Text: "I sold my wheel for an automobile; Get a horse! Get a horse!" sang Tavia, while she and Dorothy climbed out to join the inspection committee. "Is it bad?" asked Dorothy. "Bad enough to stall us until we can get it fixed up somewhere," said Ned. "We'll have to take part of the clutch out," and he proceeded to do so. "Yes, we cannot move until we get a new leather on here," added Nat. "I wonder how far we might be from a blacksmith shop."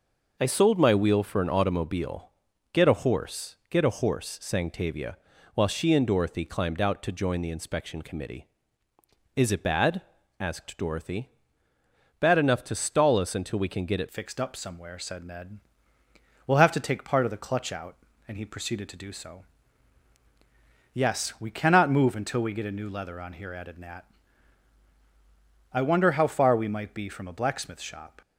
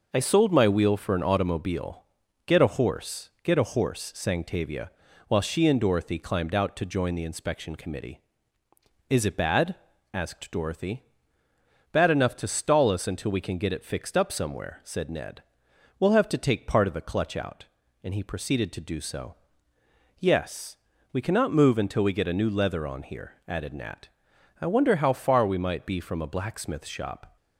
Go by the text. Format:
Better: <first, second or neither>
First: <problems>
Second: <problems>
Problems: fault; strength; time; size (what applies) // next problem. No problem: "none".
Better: second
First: changes voice at "fixed"; from 14.1 s on; 14.1 s long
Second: none